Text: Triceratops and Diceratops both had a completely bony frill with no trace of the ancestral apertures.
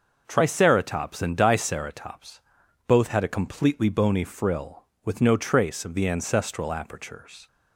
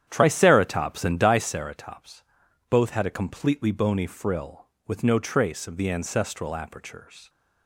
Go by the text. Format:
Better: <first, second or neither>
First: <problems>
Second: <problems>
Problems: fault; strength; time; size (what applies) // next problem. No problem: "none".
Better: first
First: pauses between "Diceratops" and "both"; noticeable; at 2.4 s; 0.46 s long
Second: starts louder than the rest; strong; until 1.4 s; 10 dB // pauses between "Diceratops" and "both"; noticeable; at 2.2 s; 0.46 s long